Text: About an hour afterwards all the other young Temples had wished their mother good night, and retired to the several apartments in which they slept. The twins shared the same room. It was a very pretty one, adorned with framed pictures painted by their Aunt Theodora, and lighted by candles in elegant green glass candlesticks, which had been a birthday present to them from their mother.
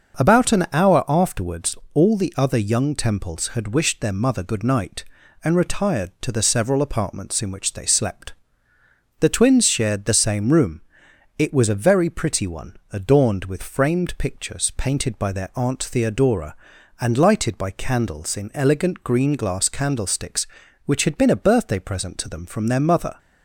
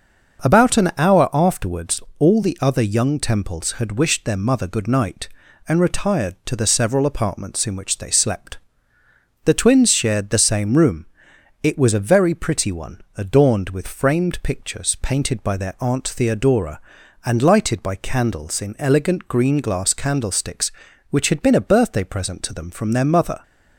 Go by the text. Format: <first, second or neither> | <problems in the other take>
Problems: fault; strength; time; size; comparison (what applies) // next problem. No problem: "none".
neither | starts louder than the rest; noticeable; the same in both // pauses between "afterwards" and "all"; slight; the same in both